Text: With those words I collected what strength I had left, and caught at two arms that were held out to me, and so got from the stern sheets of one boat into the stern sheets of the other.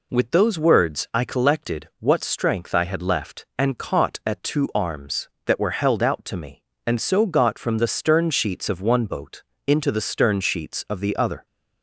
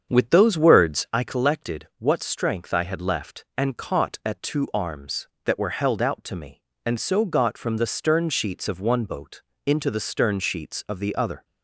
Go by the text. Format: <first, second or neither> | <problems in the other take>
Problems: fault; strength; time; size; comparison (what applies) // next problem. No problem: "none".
first | starts louder than the rest; strong; until 1.3 s; 7.5 dB // pauses between "boat" and "into"; slight; at 9.4 s; 0.24 s long; slight in the first